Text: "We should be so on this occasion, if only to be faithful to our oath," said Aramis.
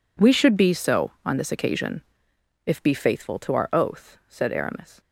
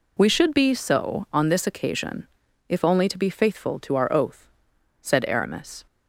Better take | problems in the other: second | skips "only to"; at 2.8 s

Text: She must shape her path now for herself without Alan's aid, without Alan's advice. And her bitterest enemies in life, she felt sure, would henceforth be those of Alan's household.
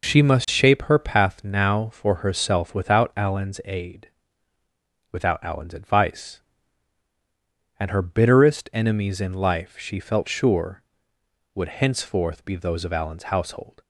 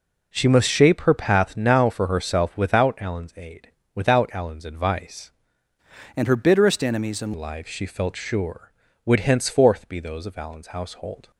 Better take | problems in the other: first | changes voice from "And" to "in"; from 6.1 to 7.3 s; 1.2 s long

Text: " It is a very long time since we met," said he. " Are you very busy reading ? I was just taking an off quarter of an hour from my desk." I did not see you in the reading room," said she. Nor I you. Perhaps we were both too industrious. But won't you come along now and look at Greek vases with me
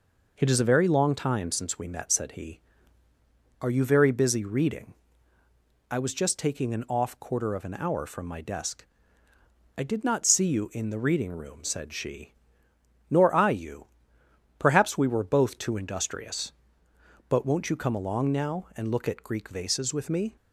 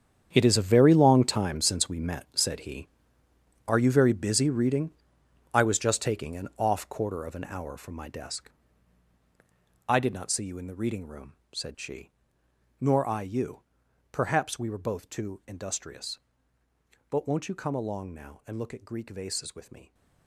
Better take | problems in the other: first | gets quieter; strong; throughout; 11 dB

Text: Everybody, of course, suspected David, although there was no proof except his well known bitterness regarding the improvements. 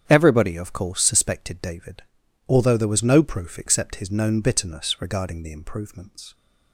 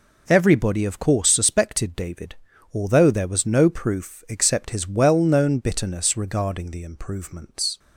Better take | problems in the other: second | starts louder than the rest; strong; until 1.0 s; 8.5 dB // skips "well"; at 4.1 s

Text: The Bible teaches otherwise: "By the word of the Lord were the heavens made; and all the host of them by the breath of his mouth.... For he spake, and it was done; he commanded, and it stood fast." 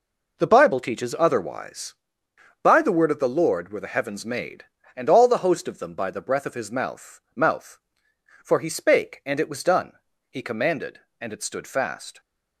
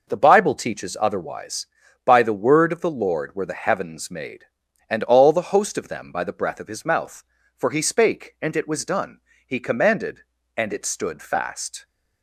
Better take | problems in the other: second | says "mouth" twice; at 7.3 s

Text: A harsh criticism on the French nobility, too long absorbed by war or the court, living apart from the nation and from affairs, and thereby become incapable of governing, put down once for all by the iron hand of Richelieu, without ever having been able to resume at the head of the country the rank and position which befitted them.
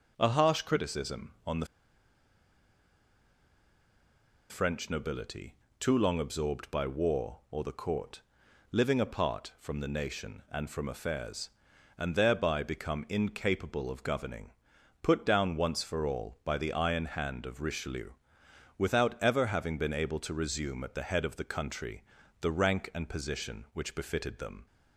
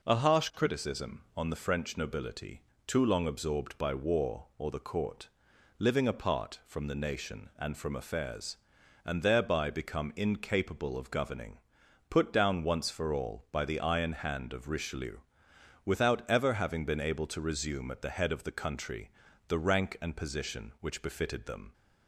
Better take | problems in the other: second | pauses between "the" and "French"; strong; at 1.6 s; 2.8 s long // pauses between "country" and "the"; at 22.0 s; 0.38 s long; also in the second

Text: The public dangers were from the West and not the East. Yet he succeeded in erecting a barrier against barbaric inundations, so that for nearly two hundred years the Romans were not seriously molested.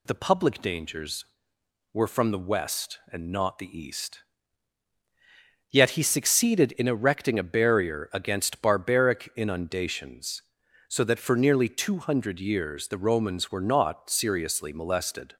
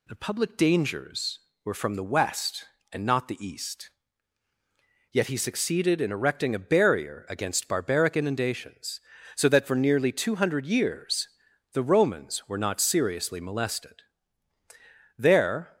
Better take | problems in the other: first | pauses between "years" and "the"; noticeable; at 11.2 s; 0.46 s long // goes on to say "There"; from 15.1 s on; 0.60 s long

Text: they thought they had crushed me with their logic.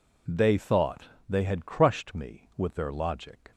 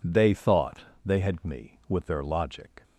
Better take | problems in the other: first | pauses between "thought" and "they"; slight; at 0.7 s; 0.26 s long; slight in the first // skips "crushed"; at 1.4 s

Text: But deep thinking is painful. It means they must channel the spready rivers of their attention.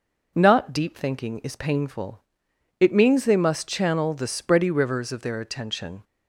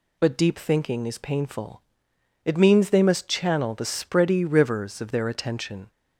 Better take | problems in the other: second | says "Not" for "But"; at 0.3 s

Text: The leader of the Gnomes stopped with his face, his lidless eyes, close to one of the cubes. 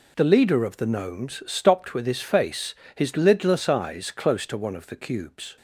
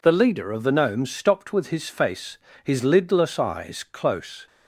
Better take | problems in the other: first | stops before "to one of the cubes"; at 4.4 s

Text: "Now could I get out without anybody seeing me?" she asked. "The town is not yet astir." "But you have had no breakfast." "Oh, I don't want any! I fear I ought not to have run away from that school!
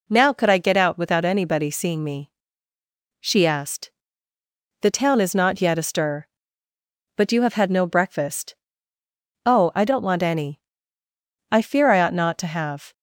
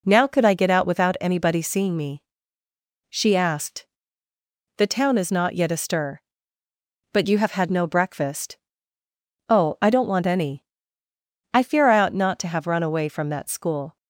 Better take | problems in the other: second | stops before "run away from that school"; at 12.9 s

